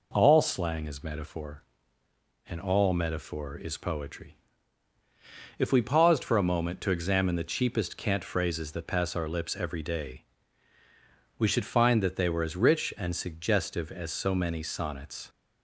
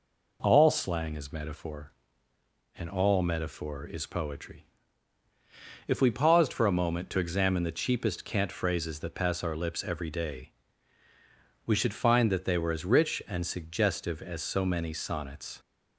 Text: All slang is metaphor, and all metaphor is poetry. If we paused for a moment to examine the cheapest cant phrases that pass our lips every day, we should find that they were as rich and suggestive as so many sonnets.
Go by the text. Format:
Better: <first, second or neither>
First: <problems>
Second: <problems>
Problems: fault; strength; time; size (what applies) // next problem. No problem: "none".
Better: neither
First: none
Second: none